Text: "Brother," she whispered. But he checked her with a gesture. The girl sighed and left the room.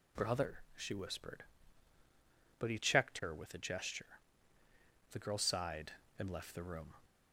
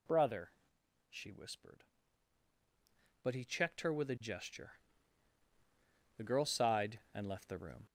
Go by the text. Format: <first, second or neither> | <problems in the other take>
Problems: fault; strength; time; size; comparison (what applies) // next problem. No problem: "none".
first | gets louder; throughout; 4 dB